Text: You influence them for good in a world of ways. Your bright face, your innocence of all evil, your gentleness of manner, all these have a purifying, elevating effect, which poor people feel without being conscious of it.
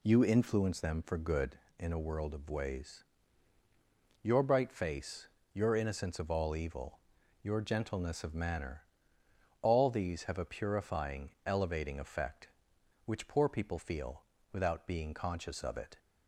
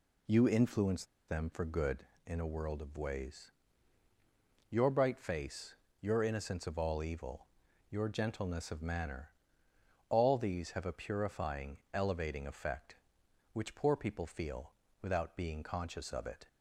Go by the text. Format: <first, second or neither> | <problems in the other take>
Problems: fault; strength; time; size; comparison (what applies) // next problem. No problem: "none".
first | pauses between "influence" and "them"; slight; at 1.0 s; 0.24 s long // pauses between "feel" and "without"; slight; at 14.7 s; 0.30 s long; slight in the first